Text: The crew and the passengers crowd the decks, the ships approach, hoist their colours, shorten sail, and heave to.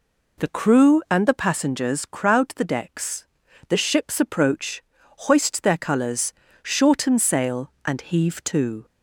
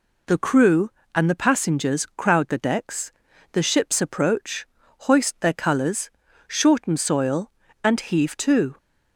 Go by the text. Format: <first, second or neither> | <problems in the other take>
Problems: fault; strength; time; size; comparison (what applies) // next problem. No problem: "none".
first | says "soil" for "sail"; at 6.9 s